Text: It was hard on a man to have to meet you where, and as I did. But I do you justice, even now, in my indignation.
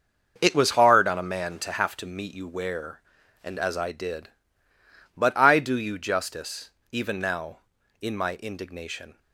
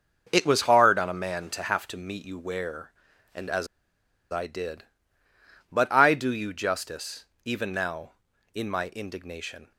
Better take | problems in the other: first | starts louder than the rest; until 1.3 s; 6.5 dB; also in the first // pauses between "as" and "I"; noticeable; at 3.6 s; 0.65 s long

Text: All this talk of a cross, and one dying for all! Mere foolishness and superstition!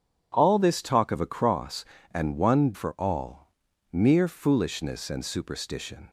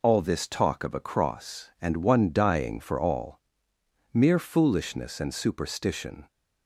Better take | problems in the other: second | starts louder than the rest; strong; until 1.3 s; 8 dB // skips "dying"; at 2.7 s

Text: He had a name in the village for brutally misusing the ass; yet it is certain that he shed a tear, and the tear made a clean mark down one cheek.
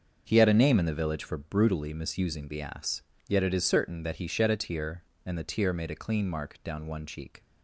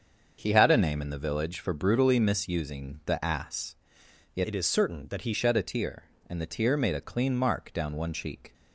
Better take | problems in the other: first | starts louder than the rest; until 1.4 s; 6.5 dB; also in the first // changes voice from "it" to "he"; from 4.4 to 5.3 s; 0.9 s long

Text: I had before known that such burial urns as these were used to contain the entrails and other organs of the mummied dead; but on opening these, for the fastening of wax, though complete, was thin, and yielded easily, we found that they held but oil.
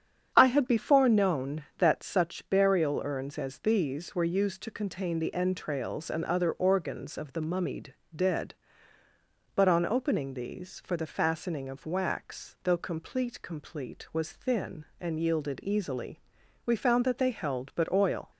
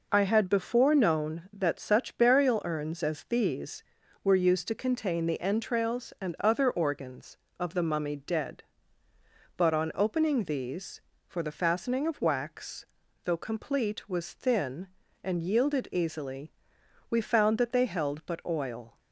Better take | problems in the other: second | starts louder than the rest; strong; until 1.3 s; 8.5 dB // pauses between "mummied" and "dead"; slight; at 7.9 s; 0.22 s long // says "complete" twice; at 13.4 s

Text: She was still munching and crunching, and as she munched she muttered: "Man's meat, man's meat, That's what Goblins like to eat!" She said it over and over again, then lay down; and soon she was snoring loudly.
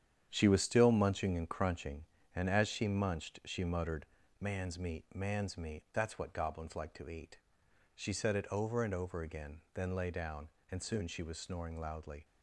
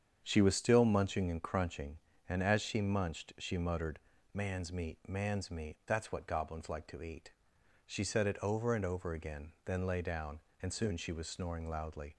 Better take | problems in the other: second | gets quieter; strong; throughout; 8 dB // starts louder than the rest; strong; until 1.3 s; 9 dB; strong in the second

